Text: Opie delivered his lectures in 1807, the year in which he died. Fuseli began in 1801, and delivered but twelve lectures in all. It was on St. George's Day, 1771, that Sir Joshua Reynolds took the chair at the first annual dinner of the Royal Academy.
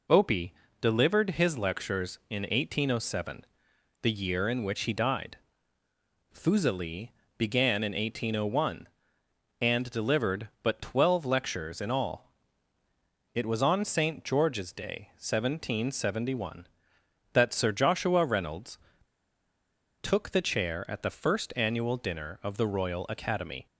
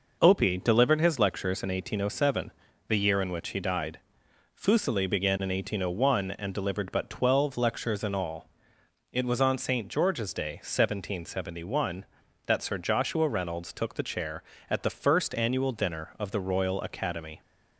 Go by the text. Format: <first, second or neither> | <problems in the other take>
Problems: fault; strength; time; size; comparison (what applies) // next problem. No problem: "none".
second | pauses between "Opie" and "delivered"; slight; at 0.5 s; 0.30 s long // pauses between "Fuseli" and "began"; slight; at 7.1 s; 0.26 s long // pauses between "Reynolds" and "took"; strong; at 18.7 s; 1.2 s long